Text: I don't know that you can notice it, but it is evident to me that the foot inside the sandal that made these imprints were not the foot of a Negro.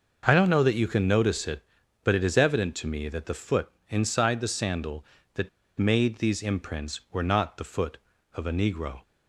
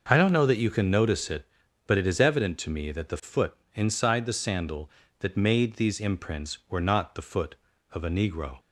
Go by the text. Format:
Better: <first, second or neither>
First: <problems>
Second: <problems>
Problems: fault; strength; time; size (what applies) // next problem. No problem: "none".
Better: second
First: pauses between "foot" and "inside"; slight; at 3.6 s; 0.22 s long // pauses between "that" and "made"; slight; at 5.4 s; 0.30 s long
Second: pauses between "foot" and "inside"; slight; at 3.5 s; 0.22 s long